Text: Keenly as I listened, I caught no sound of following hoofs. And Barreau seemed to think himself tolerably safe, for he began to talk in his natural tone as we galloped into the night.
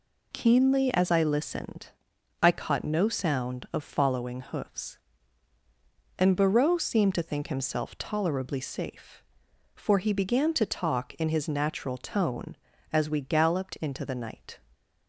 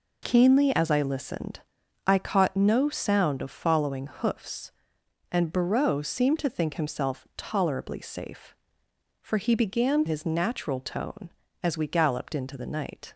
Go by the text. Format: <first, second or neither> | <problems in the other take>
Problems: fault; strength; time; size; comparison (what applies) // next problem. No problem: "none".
first | skips "to talk in"; at 10.0 s